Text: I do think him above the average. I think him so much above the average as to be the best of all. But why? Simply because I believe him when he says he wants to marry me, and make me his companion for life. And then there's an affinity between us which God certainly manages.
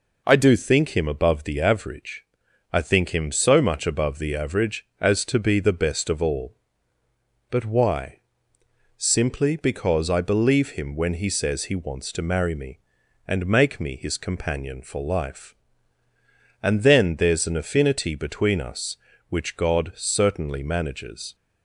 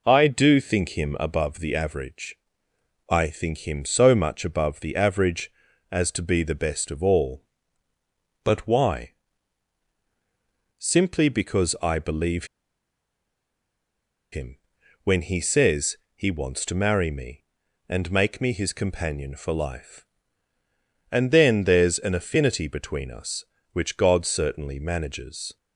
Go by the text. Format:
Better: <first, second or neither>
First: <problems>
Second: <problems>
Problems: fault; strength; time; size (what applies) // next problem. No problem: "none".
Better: first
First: none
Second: pauses between "believe" and "him"; strong; at 12.4 s; 1.8 s long // pauses between "him" and "when"; noticeable; at 14.5 s; 0.48 s long // pauses between "says" and "he"; slight; at 15.9 s; 0.20 s long